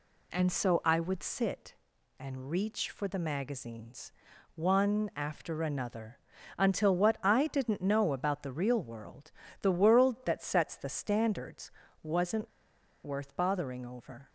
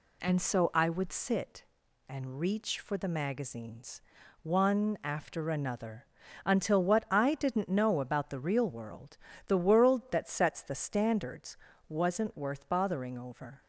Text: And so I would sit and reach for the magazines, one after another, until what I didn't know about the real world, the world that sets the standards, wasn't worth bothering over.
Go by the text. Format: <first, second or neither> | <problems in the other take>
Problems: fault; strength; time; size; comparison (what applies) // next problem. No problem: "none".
second | pauses between "wasn't" and "worth"; noticeable; at 12.5 s; 0.53 s long